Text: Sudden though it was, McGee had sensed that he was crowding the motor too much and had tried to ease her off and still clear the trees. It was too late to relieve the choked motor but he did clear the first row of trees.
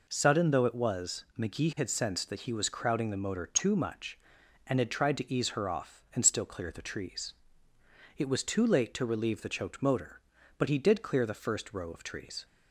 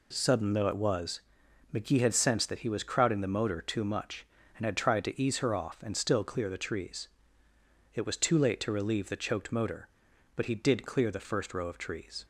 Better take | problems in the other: neither | none

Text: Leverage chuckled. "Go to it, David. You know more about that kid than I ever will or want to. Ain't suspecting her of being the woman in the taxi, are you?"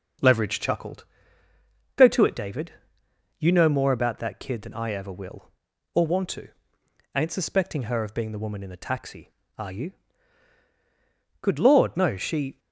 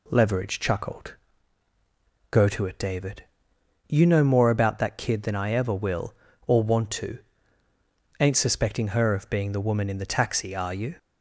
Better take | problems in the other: second | starts louder than the rest; until 2.1 s; 6 dB // goes on to say "Good Lord no She"; noticeable; from 11.4 s on; 1.1 s long

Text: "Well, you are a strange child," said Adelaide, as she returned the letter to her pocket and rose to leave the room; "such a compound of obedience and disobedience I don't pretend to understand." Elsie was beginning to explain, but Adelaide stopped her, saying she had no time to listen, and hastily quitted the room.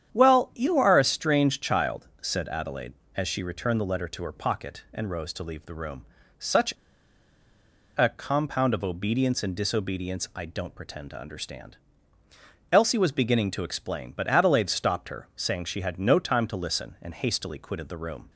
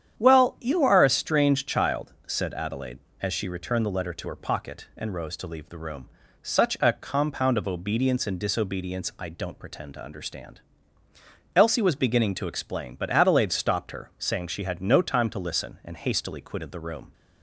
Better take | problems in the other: second | starts louder than the rest; strong; until 1.1 s; 9 dB; strong in the second // pauses between "such" and "a"; at 6.7 s; 1.2 s long

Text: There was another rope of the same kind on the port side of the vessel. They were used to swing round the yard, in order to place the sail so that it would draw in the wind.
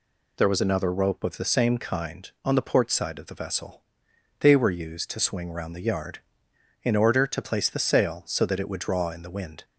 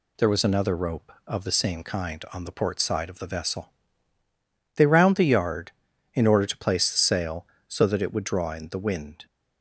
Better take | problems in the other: first | skips "were used to swing"; at 4.8 s

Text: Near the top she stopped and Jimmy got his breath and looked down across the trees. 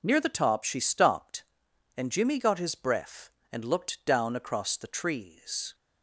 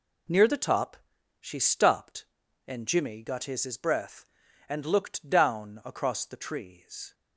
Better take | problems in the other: first | pauses between "top" and "she"; at 0.9 s; 0.42 s long // says "his" twice; at 3.6 s

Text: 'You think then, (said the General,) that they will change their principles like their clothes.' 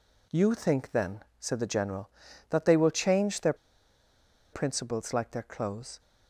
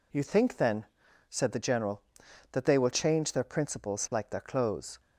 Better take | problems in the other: second | pauses between "their" and "principles"; at 3.5 s; 0.98 s long

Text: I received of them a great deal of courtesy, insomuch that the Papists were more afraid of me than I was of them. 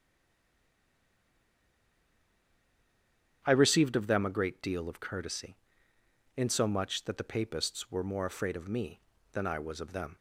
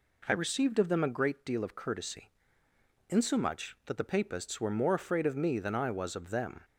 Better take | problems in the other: second | stays silent before the first word; strong; until 3.4 s; 3.4 s long // starts louder than the rest; strong; until 4.4 s; 9 dB

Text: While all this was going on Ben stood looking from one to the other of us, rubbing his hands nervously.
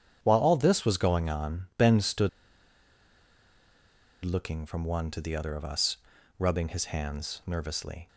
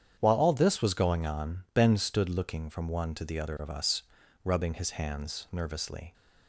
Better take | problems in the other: second | starts louder than the rest; strong; until 1.2 s; 8.5 dB; strong in the second // pauses between "stood" and "looking"; strong; at 2.2 s; 1.9 s long

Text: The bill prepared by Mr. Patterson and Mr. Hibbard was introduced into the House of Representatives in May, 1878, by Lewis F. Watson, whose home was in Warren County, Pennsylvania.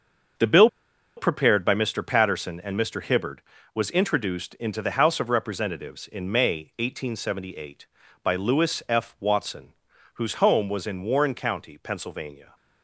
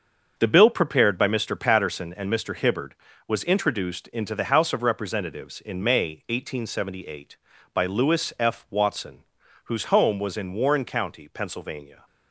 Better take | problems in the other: second | starts louder than the rest; until 1.8 s; 6.5 dB; also in the second // pauses between "bill" and "prepared"; noticeable; at 0.6 s; 0.49 s long

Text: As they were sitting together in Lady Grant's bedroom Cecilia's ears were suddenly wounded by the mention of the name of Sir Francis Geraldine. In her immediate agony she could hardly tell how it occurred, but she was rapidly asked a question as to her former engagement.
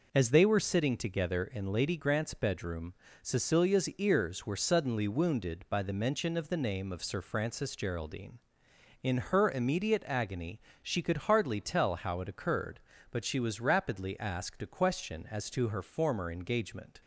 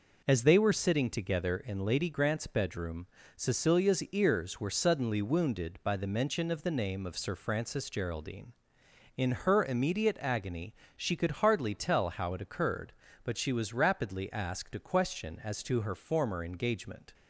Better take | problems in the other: neither | pauses between "bedroom" and "Cecilia's"; slight; the same in both // pauses between "agony" and "she"; slight; the same in both

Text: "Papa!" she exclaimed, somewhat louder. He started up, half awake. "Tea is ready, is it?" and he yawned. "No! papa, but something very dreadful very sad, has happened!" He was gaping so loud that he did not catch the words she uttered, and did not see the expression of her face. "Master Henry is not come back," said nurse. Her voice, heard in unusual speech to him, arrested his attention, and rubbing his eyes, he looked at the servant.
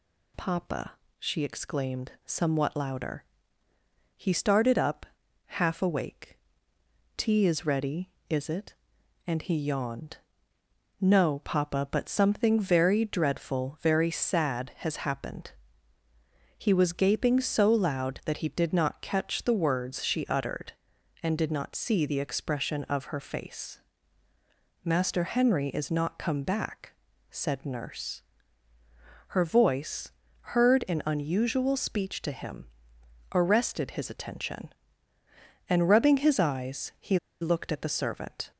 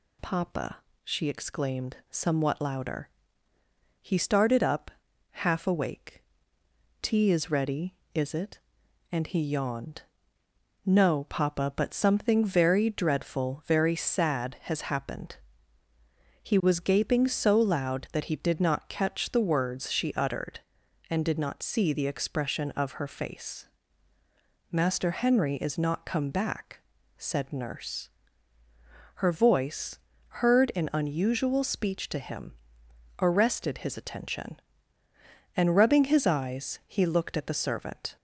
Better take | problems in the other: second | pauses between "he" and "looked"; slight; at 37.1 s; 0.24 s long

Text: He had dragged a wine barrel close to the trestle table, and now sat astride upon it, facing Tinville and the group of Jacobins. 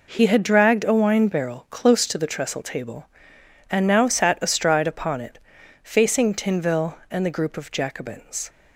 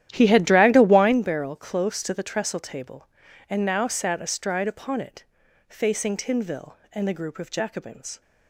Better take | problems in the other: first | starts louder than the rest; strong; until 1.2 s; 11.5 dB

